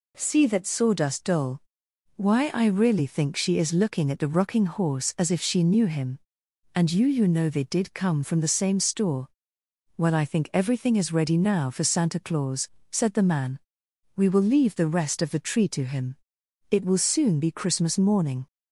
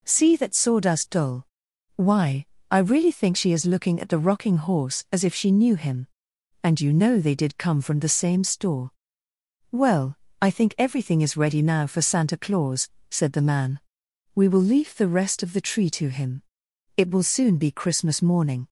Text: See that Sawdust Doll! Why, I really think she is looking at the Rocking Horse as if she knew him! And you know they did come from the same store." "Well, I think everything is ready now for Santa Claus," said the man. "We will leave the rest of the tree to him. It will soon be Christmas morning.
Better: second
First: says "you" twice; at 7.0 s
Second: none

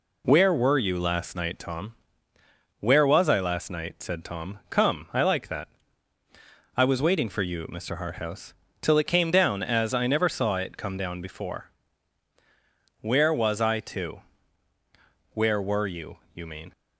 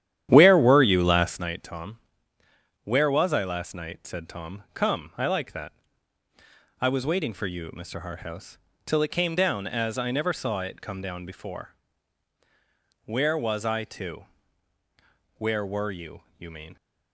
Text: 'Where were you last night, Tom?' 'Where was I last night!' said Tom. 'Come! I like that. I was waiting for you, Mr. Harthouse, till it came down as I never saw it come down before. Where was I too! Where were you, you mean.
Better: first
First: none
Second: starts louder than the rest; strong; until 1.5 s; 11 dB

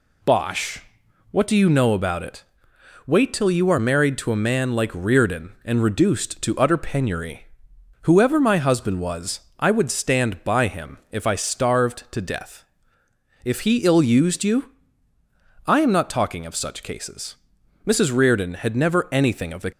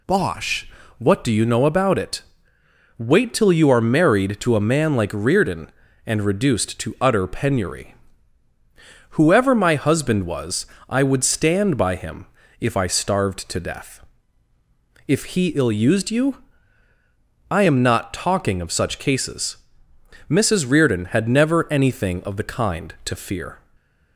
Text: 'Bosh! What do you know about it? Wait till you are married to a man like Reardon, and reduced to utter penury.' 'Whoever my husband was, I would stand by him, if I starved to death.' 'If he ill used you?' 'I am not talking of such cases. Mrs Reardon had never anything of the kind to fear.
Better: second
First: stops before "kind to fear"; at 19.7 s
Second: none

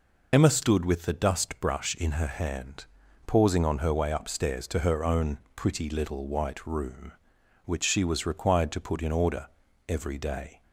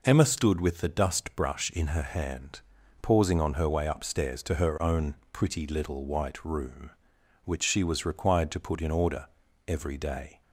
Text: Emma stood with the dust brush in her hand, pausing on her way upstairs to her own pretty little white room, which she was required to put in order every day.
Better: second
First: loses the start of "Emma"; at 0.3 s; 45 ms // pauses between "own" and "pretty"; slight; at 5.3 s; 0.16 s long // pauses between "order" and "every"; at 9.4 s; 0.38 s long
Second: pauses between "own" and "pretty"; slight; at 5.1 s; 0.16 s long // pauses between "order" and "every"; at 9.2 s; 0.38 s long

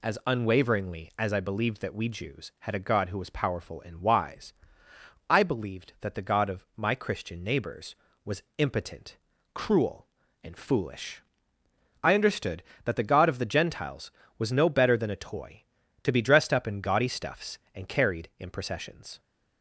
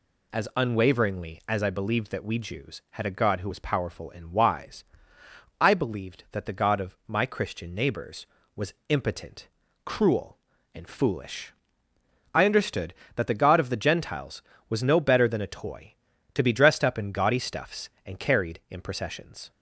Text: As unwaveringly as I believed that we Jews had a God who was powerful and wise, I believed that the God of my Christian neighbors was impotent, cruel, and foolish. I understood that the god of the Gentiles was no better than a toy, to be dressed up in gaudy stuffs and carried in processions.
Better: neither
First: none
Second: none

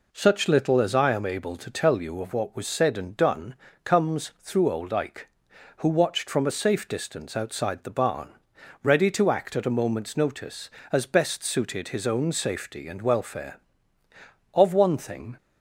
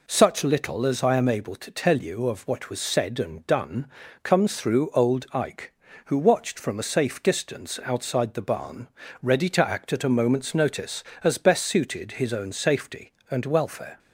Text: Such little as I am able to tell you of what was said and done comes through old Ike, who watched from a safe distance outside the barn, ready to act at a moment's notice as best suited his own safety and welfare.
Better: second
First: pauses between "done" and "comes"; slight; at 3.5 s; 0.30 s long // goes on to say "Of one thing"; noticeable; from 14.5 s on; 0.84 s long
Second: pauses between "done" and "comes"; slight; at 3.8 s; 0.36 s long

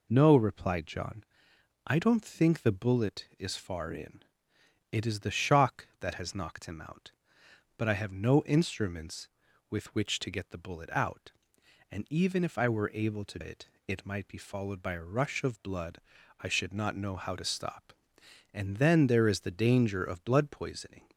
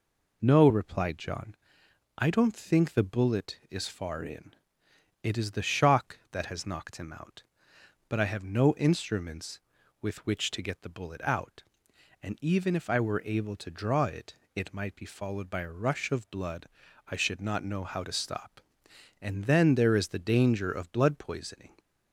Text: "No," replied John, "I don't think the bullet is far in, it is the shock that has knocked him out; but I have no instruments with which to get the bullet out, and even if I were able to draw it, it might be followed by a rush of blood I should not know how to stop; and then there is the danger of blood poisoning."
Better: second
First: skips "draw"; at 13.4 s // pauses between "blood" and "I"; at 15.9 s; 0.40 s long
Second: pauses between "blood" and "I"; at 16.6 s; 0.40 s long

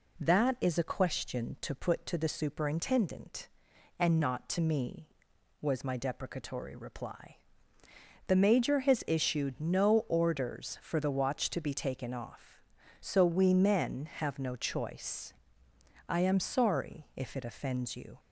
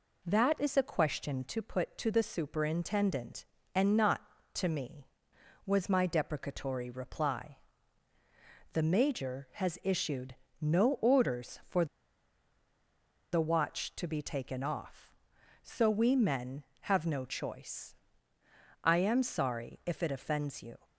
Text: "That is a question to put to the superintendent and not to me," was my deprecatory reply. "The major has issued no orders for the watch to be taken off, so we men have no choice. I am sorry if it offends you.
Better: first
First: none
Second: pauses between "issued" and "no"; slight; at 10.3 s; 0.26 s long // pauses between "for" and "the"; strong; at 11.8 s; 1.4 s long

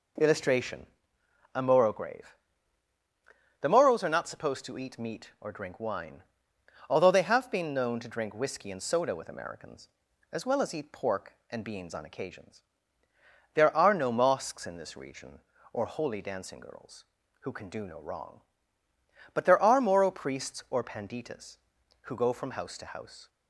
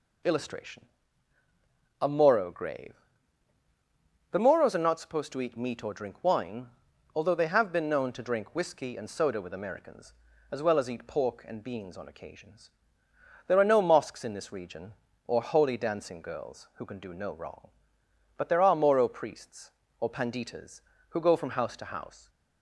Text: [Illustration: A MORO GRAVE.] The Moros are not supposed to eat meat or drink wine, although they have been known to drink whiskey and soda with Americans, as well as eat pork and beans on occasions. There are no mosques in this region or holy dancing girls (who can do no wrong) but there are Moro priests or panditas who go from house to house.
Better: neither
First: none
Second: none

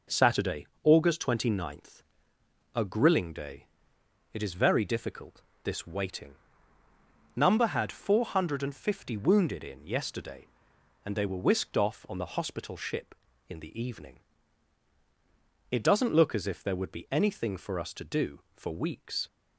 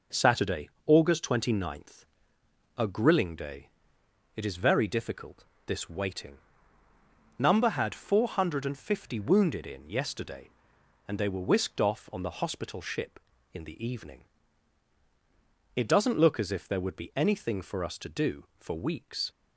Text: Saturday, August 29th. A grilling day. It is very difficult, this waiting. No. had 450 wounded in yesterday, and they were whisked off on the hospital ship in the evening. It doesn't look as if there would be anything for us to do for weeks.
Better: neither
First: none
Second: none

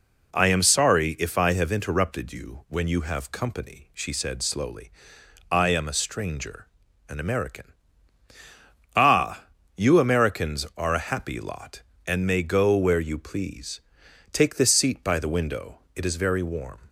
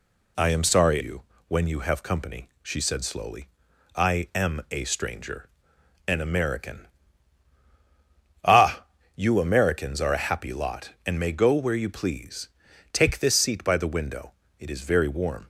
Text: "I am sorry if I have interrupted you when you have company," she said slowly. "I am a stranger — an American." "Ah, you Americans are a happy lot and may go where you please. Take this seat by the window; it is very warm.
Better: first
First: none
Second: skips "if I have interrupted"; at 0.9 s // pauses between "you" and "when"; slight; at 1.2 s; 0.24 s long

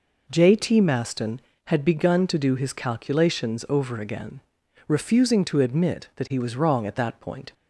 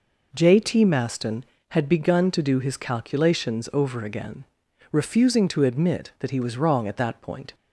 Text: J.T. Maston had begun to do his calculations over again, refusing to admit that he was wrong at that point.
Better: neither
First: none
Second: none

